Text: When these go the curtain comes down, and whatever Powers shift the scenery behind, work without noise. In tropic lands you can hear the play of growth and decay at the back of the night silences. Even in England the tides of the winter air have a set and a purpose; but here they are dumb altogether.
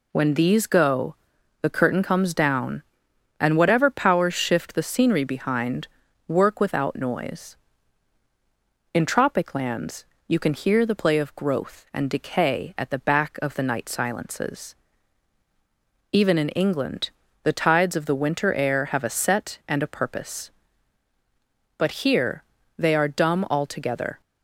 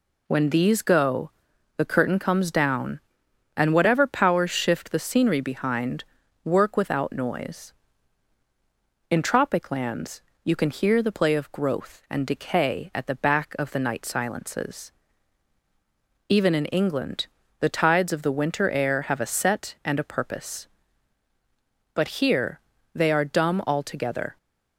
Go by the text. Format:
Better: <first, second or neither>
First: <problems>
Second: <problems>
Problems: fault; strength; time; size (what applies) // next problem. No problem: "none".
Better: neither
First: pauses between "go" and "the"; noticeable; at 1.1 s; 0.46 s long // pauses between "lands" and "you"; slight; at 10.0 s; 0.24 s long // pauses between "England" and "the"; slight; at 17.1 s; 0.32 s long // pauses between "here" and "they"; slight; at 22.4 s; 0.34 s long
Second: pauses between "go" and "the"; noticeable; at 1.2 s; 0.46 s long // pauses between "lands" and "you"; slight; at 10.2 s; 0.24 s long // pauses between "England" and "the"; slight; at 17.2 s; 0.32 s long // pauses between "here" and "they"; slight; at 22.6 s; 0.34 s long